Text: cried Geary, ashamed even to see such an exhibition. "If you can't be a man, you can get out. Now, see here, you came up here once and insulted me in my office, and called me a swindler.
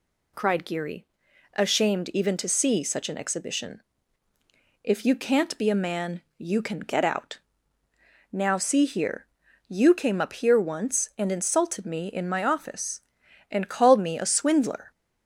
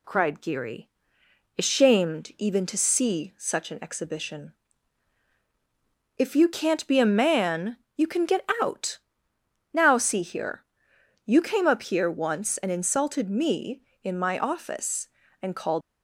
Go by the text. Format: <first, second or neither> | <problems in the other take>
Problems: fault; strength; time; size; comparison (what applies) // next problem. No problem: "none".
first | stops before "me a swindler"; at 15.8 s